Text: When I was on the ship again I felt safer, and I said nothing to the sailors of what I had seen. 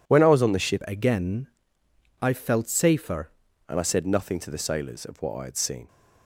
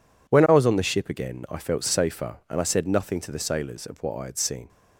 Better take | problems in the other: second | changes voice from "again" to "safer"; from 0.8 to 3.3 s; 2.5 s long // pauses between "again" and "I"; noticeable; at 1.4 s; 0.76 s long

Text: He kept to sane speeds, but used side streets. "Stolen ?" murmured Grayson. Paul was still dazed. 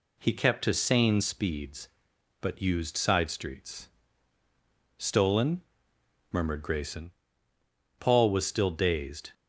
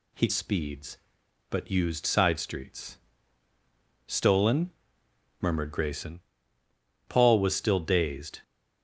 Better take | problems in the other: first | skips "kept to sane"; at 0.2 s

